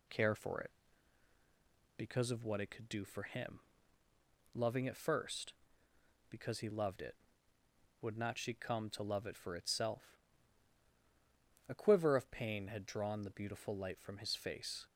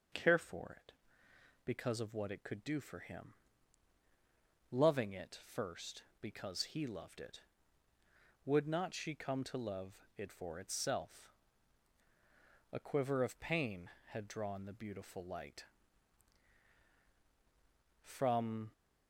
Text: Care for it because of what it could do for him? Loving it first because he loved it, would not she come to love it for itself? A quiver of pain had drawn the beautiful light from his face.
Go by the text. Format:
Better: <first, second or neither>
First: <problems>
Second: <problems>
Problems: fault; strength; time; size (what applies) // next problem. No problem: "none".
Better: first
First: none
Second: starts louder than the rest; noticeable; until 1.8 s; 6 dB // pauses between "love" and "it"; slight; at 9.9 s; 0.18 s long // stops before "his face"; at 18.7 s